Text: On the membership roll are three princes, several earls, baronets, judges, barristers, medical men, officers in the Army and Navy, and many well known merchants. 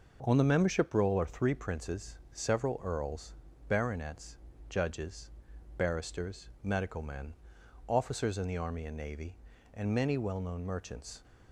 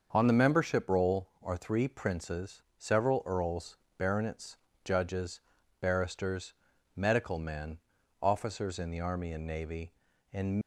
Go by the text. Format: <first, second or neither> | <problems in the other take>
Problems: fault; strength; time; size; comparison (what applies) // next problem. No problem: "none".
first | starts louder than the rest; until 1.1 s; 6.5 dB // stops before "many well known merchants"; at 10.6 s